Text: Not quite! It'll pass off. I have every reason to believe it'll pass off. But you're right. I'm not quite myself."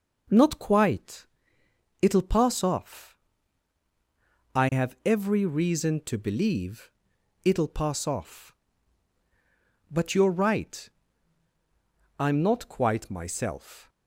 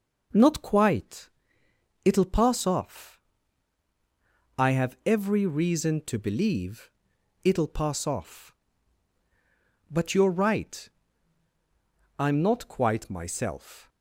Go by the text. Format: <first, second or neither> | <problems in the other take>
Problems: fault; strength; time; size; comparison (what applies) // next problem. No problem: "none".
neither | pauses between "believe" and "it'll"; noticeable; the same in both